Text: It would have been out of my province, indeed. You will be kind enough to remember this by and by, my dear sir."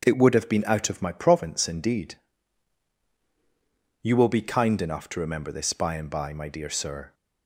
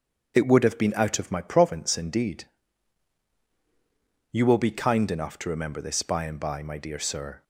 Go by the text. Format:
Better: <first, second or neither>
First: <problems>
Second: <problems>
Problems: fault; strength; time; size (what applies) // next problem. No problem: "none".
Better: first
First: starts louder than the rest; strong; until 1.0 s; 7.5 dB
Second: loses the start of "It"; at 0.3 s; 20 ms // starts louder than the rest; strong; until 1.3 s; 7 dB